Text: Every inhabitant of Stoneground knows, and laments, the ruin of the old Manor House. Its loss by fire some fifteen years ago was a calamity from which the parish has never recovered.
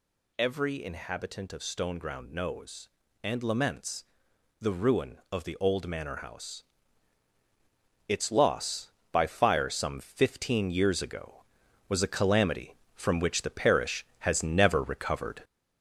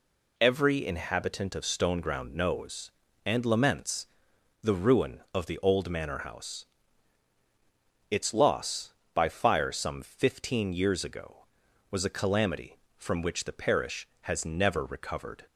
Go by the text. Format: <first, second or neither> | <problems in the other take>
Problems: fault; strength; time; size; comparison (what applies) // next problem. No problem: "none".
second | gets louder; noticeable; throughout; 4.5 dB